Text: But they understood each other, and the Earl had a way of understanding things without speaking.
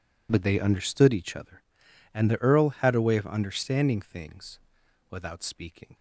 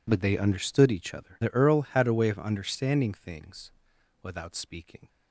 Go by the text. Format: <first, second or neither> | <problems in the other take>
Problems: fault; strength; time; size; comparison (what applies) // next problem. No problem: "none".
first | skips "and"; at 1.4 s // pauses between "things" and "without"; noticeable; at 3.7 s; 0.50 s long; noticeable in the first